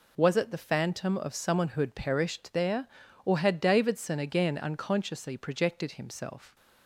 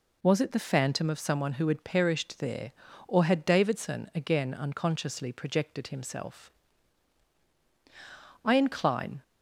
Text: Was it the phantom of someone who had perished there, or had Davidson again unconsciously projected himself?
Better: first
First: none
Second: goes on to say "I incline"; noticeable; from 8.4 s on; 0.78 s long

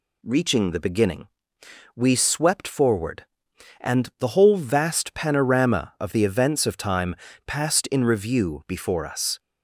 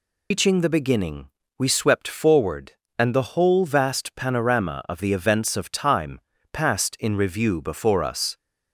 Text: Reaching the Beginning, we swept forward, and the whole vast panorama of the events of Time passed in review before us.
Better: first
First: pauses between "Time" and "passed"; slight; at 7.1 s; 0.32 s long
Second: loses the start of "Reaching"; at 0.3 s; 115 ms // pauses between "Time" and "passed"; slight; at 6.1 s; 0.32 s long

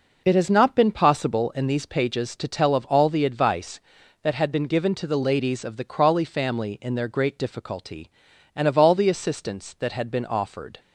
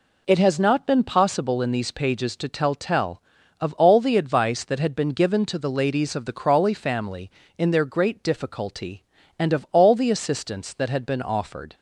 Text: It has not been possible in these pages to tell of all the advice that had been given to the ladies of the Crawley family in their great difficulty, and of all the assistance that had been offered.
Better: first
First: none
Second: says "tell" twice; at 2.7 s

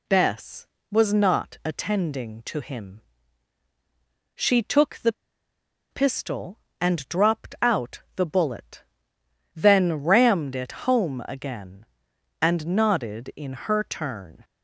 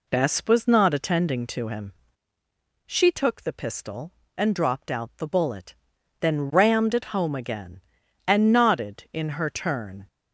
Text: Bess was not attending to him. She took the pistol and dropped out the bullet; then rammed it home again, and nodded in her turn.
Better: second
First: pauses between "the" and "pistol"; noticeable; at 5.1 s; 0.79 s long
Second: none

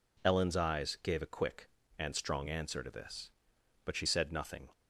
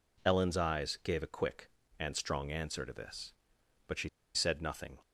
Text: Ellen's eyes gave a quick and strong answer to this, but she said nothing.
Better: first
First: none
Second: pauses between "she" and "said"; slight; at 4.0 s; 0.26 s long

